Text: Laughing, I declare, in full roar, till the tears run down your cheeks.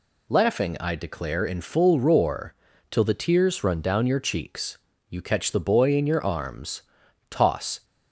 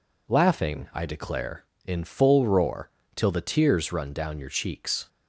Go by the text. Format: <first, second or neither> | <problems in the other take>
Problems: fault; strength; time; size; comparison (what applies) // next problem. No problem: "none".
second | goes on to say "You catch the boy in your arms toss"; strong; from 5.1 s on; 2.7 s long